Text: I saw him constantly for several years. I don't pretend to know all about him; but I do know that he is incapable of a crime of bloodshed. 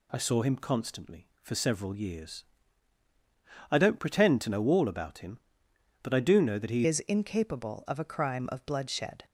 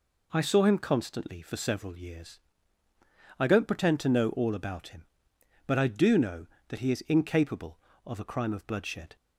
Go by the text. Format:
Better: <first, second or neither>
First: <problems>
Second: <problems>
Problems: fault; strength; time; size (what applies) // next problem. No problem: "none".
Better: second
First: changes voice at "is"; from 6.8 s on; 2.4 s long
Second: none